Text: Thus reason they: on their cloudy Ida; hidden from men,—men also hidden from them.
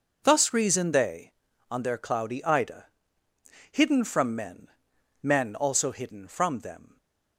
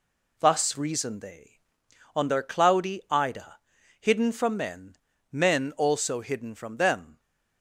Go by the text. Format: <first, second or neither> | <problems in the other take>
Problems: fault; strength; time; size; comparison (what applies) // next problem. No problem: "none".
neither | none